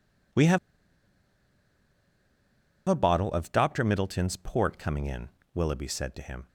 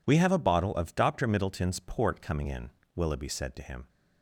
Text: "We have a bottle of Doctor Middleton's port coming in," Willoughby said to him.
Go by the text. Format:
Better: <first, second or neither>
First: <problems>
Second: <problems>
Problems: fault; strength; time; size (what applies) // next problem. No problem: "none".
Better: second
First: pauses between "have" and "a"; strong; at 0.5 s; 2.3 s long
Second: none